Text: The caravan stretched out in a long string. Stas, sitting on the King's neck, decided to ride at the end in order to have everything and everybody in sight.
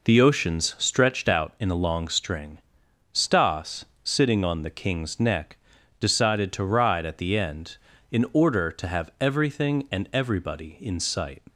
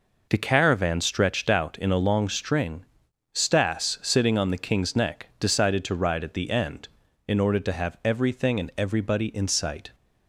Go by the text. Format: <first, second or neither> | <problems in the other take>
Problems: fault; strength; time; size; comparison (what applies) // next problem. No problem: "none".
second | says "oceans" for "caravan"; at 0.1 s